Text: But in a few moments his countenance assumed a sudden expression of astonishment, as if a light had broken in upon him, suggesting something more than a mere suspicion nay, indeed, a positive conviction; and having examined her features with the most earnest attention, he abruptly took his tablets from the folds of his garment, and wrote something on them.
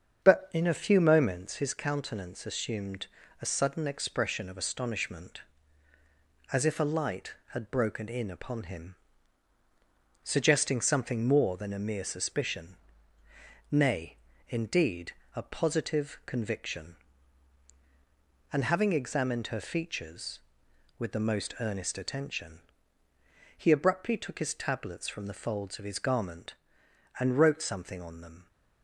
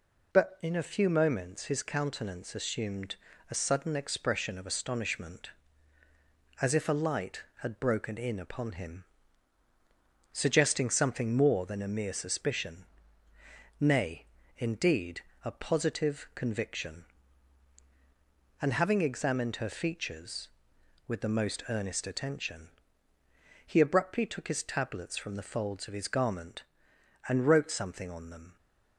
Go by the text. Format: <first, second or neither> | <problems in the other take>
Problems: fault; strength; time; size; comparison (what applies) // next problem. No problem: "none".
second | starts louder than the rest; strong; until 1.7 s; 7.5 dB // pauses between "assumed" and "a"; slight; at 3.0 s; 0.34 s long; slight in the second // pauses between "suspicion" and "nay"; noticeable; at 12.7 s; 0.94 s long; noticeable in the second